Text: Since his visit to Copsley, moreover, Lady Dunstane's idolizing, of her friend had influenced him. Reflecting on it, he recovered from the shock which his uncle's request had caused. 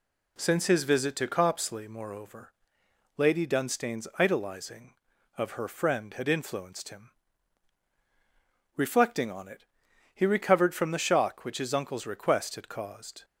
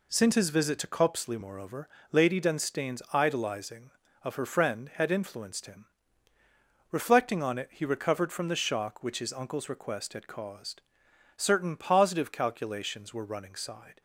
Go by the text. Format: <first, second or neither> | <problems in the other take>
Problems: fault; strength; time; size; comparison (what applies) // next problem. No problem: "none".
first | goes on to say "Certain positive calculations were running side"; strong; from 11.3 s on; 2.6 s long